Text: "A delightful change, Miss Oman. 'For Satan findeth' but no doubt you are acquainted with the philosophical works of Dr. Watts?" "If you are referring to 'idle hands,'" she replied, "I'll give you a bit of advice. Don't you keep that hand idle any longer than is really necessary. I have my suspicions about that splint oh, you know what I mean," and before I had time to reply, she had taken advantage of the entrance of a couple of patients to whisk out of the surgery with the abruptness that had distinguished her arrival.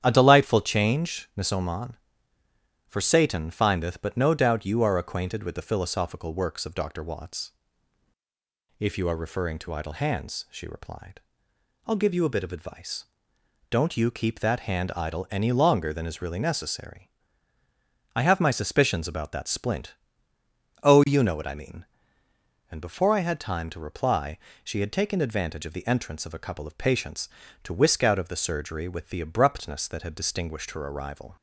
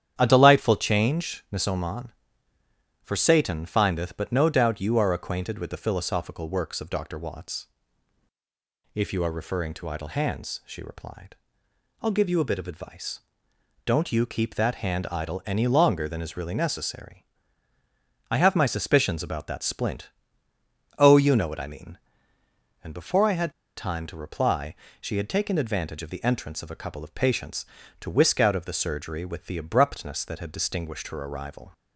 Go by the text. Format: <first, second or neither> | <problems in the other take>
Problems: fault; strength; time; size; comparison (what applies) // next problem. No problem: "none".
first | starts louder than the rest; strong; until 1.1 s; 9.5 dB; strong in the first // pauses between "splint" and "oh"; noticeable; at 20.1 s; 0.88 s long; noticeable in the first // pauses between "had" and "time"; slight; at 23.5 s; 0.26 s long